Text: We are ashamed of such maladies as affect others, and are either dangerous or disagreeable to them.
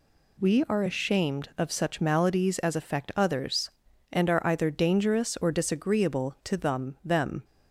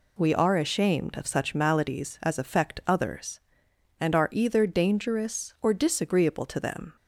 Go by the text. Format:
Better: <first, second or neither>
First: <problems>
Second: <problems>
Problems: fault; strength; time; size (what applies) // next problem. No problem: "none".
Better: second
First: says "them" twice; at 7.0 s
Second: none